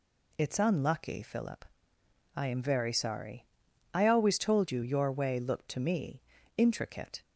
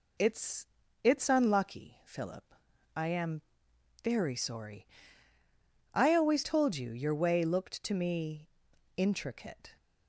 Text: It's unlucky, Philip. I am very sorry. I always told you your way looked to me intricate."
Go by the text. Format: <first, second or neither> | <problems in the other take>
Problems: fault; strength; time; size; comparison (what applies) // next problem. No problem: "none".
first | says "It's" twice; at 1.0 s // pauses between "am" and "very"; noticeable; at 3.4 s; 0.62 s long // pauses between "me" and "intricate"; noticeable; at 8.4 s; 0.48 s long; slight in the first